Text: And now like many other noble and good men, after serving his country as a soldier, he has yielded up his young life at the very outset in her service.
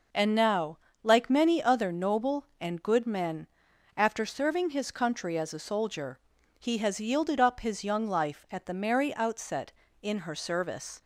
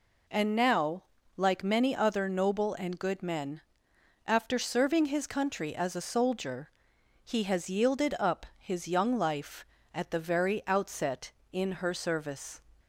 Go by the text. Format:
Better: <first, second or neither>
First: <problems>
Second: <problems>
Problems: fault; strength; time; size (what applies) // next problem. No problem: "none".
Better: second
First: pauses between "now" and "like"; slight; at 0.7 s; 0.26 s long // says "merry" for "very"; at 8.7 s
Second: pauses between "now" and "like"; slight; at 1.0 s; 0.34 s long